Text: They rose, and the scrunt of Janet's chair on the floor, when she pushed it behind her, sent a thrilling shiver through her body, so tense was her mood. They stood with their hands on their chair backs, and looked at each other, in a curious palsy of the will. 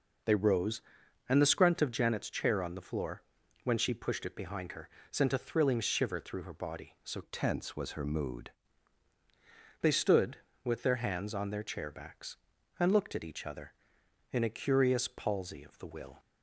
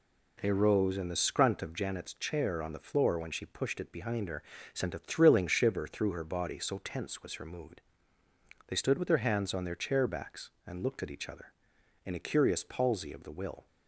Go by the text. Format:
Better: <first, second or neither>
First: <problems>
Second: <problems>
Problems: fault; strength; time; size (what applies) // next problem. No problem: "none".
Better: second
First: changes voice from "tense" to "mood"; from 7.2 to 8.5 s; 1.3 s long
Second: none